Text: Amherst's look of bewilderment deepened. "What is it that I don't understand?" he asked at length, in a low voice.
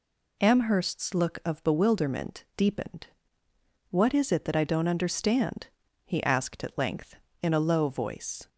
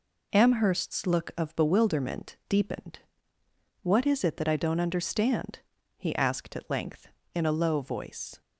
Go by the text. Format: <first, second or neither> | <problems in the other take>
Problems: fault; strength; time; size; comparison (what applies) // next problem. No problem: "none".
first | gets quieter; noticeable; throughout; 5.5 dB